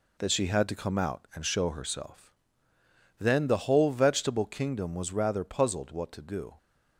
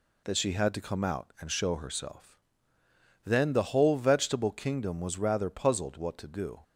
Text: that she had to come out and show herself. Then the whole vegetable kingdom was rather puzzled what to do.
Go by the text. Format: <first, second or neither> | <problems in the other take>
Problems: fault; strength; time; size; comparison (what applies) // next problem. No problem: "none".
second | gets quieter; noticeable; throughout; 6 dB